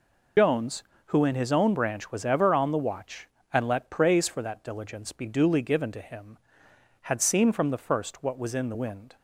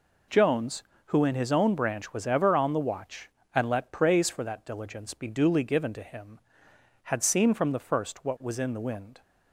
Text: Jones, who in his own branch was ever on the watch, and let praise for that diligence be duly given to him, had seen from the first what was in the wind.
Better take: second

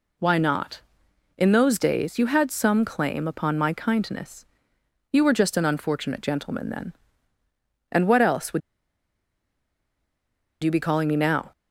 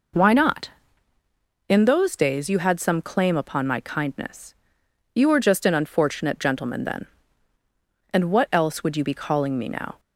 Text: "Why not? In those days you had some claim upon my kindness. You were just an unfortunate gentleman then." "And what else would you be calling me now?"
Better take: second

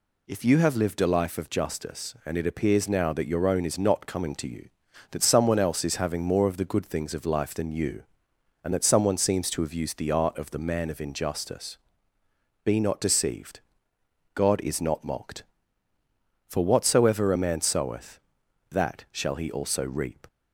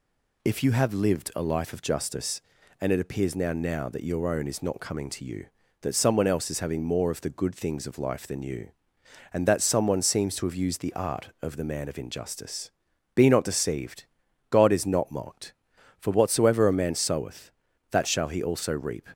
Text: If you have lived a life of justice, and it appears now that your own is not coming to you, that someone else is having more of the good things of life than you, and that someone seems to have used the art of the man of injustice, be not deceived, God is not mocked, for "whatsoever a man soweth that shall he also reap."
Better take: first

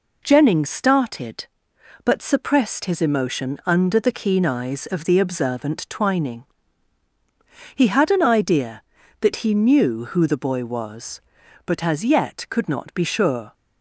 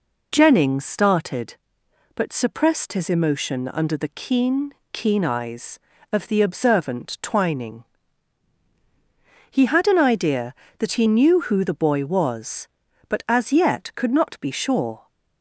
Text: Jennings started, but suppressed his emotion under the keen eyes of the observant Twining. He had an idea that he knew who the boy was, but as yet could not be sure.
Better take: first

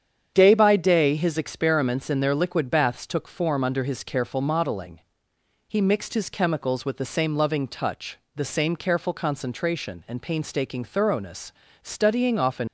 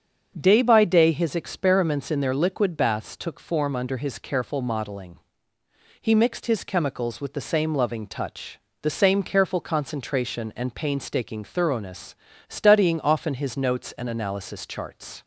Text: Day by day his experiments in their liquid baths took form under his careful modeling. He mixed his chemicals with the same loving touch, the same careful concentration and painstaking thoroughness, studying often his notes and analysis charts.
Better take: second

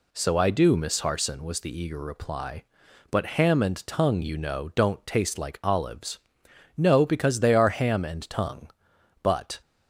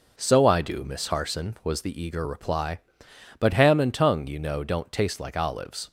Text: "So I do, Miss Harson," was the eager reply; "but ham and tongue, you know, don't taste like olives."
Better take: second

